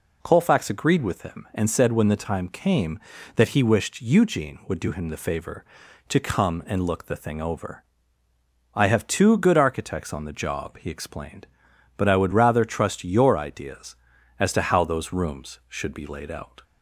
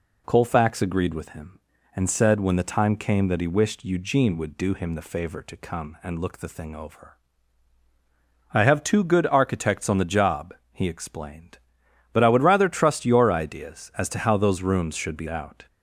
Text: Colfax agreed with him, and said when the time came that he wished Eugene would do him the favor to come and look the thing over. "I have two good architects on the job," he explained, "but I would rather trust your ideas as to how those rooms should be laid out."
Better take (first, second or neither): first